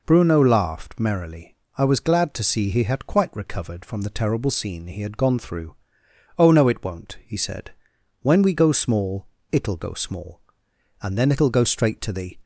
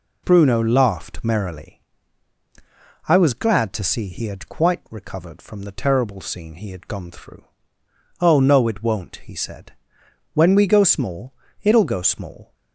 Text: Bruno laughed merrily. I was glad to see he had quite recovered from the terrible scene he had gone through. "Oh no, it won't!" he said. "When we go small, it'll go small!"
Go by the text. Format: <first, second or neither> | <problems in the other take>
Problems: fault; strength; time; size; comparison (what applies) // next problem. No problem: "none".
second | goes on to say "And then it'll go straight to the"; from 11.0 s on; 1.3 s long